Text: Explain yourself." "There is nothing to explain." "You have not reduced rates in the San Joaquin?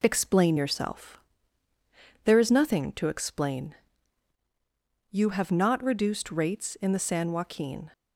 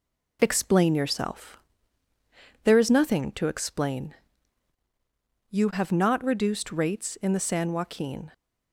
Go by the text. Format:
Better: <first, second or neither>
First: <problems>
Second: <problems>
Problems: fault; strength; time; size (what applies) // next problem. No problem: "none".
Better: neither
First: none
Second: none